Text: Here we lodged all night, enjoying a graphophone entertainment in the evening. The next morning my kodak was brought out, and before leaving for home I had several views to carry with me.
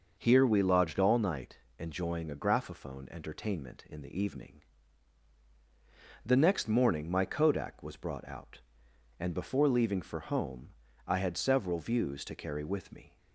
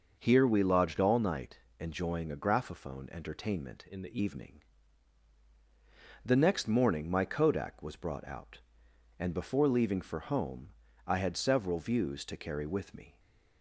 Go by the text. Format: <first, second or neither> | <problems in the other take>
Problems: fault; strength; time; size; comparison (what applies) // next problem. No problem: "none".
first | changes voice from "in" to "the"; from 3.8 to 4.1 s; 0.3 s long // pauses between "home" and "I"; slight; at 10.6 s; 0.36 s long; slight in the first // stays silent after the last word; slight; from 13.1 s on; 0.5 s long